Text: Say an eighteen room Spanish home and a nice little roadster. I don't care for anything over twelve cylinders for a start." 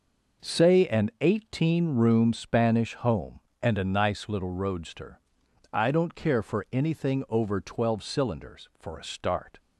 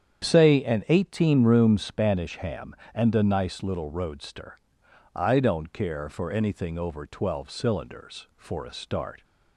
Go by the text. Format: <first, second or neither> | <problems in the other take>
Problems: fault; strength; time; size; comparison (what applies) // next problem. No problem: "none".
first | starts louder than the rest; strong; until 1.2 s; 8.5 dB // says "ham" for "home"; at 2.3 s